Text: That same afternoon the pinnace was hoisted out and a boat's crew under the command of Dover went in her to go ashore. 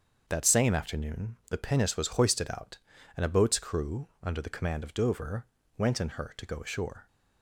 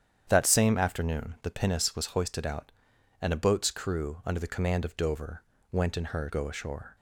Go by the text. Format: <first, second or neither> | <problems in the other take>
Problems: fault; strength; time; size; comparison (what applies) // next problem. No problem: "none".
first | starts louder than the rest; strong; until 1.2 s; 9 dB; strong in the first // pauses between "Dover" and "went"; slight; at 5.4 s; 0.30 s long; slight in the first // skips "to"; at 6.3 s